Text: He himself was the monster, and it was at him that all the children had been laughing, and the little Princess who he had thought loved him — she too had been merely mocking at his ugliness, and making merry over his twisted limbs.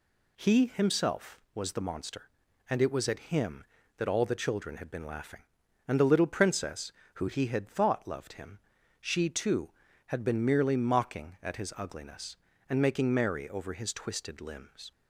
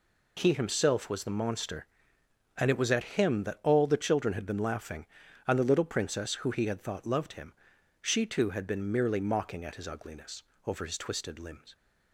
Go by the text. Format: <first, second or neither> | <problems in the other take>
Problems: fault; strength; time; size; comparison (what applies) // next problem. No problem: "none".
first | skips "and making merry"; at 10.5 s